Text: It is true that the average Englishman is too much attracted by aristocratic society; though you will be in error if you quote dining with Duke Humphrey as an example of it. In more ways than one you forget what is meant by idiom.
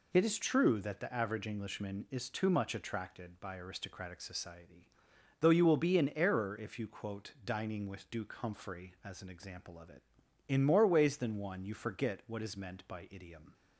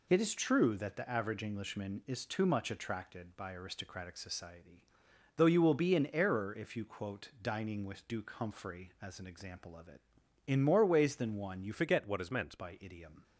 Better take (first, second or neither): first